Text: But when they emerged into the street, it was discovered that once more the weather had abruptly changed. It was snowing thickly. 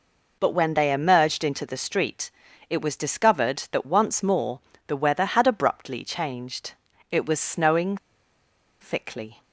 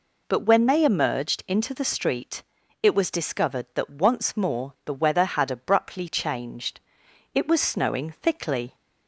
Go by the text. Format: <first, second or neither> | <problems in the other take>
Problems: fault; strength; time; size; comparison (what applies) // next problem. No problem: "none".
second | pauses between "more" and "the"; slight; at 4.6 s; 0.26 s long // pauses between "snowing" and "thickly"; noticeable; at 7.9 s; 0.84 s long